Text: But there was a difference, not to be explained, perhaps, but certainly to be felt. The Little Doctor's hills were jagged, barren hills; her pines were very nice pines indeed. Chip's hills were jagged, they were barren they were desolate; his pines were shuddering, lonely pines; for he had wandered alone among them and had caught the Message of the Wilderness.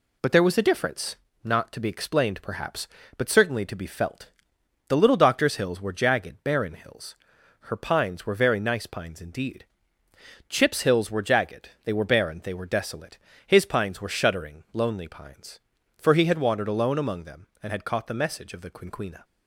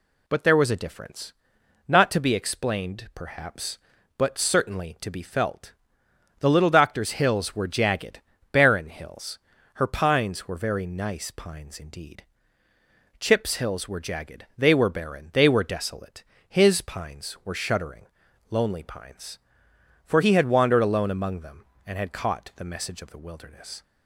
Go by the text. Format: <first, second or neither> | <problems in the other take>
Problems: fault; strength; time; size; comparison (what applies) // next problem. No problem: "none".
second | says "Quinquina" for "Wilderness"; at 18.6 s